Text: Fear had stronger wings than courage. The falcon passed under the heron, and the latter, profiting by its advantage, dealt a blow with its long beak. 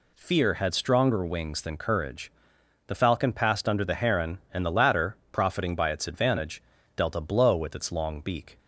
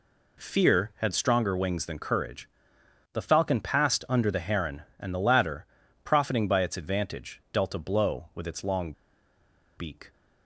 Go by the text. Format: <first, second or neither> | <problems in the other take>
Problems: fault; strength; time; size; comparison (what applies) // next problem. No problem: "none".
first | pauses between "long" and "beak"; noticeable; at 8.9 s; 0.84 s long